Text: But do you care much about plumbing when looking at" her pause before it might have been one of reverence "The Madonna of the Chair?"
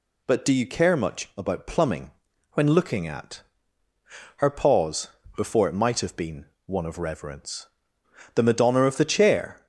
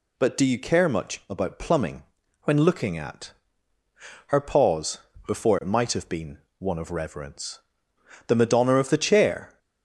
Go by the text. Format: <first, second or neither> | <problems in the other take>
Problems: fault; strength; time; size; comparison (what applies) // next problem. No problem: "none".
neither | pauses between "plumbing" and "when"; the same in both // pauses between "at" and "her"; noticeable; the same in both // pauses between "pause" and "before"; slight; the same in both // pauses between "been" and "one"; slight; the same in both // pauses between "reverence" and "The"; noticeable; the same in both